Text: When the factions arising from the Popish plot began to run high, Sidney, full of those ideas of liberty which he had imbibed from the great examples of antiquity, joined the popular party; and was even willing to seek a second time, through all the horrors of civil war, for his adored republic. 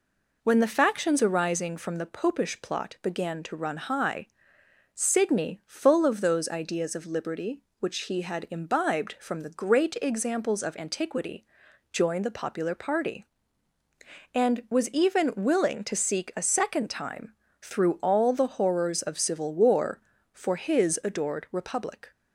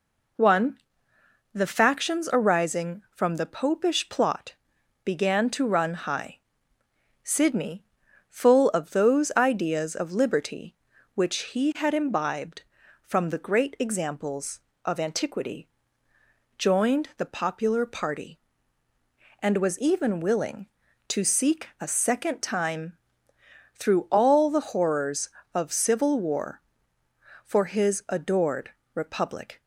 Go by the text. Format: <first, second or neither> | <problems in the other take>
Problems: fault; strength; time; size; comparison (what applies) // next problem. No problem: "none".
first | says "One" for "When"; at 0.3 s // pauses between "plot" and "began"; noticeable; at 4.5 s; 0.52 s long // pauses between "adored" and "republic"; slight; at 28.7 s; 0.24 s long